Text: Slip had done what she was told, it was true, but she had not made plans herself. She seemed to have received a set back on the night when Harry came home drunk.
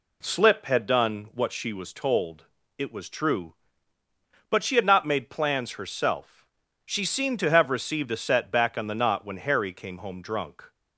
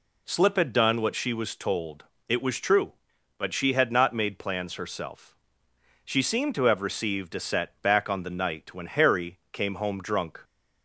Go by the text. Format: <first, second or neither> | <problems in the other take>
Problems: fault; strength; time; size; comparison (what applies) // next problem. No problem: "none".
second | says "knot" for "night"; at 8.9 s